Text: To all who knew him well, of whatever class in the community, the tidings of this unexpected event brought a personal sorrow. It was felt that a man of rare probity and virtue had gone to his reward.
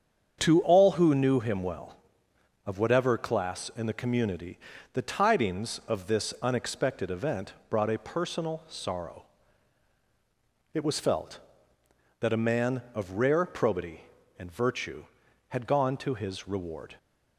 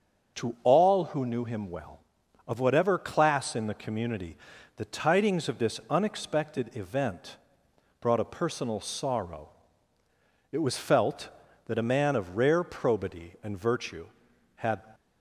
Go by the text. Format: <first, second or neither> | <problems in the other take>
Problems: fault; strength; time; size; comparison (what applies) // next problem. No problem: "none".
first | starts louder than the rest; noticeable; until 1.4 s; 6 dB; strong in the first // pauses between "event" and "brought"; noticeable; at 7.3 s; 0.64 s long; slight in the first // stops before "gone to his reward"; at 14.9 s